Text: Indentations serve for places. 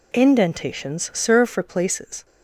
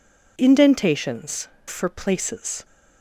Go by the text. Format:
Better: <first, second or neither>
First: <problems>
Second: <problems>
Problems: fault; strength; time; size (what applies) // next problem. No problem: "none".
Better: first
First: none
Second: skips "serve"; at 1.5 s